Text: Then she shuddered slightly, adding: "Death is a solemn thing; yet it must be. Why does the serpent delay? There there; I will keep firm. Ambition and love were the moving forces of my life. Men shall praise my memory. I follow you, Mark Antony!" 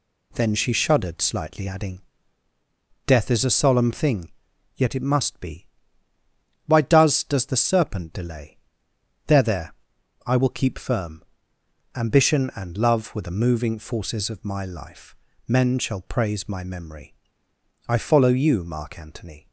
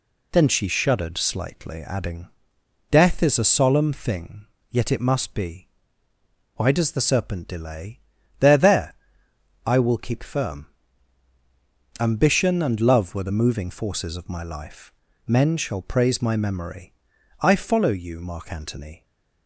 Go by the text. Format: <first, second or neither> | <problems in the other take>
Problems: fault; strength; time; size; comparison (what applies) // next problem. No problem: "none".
second | says "does" twice; at 7.2 s